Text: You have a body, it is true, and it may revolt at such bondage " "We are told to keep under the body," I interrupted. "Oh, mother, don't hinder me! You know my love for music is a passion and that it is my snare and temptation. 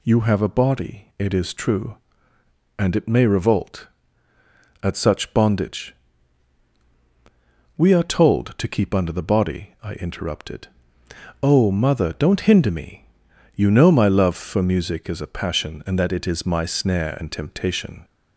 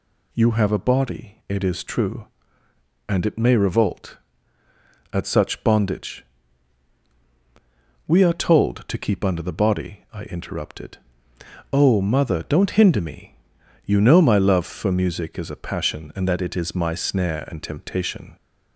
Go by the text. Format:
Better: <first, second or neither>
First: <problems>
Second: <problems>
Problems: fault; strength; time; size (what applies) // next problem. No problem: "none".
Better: neither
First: none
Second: none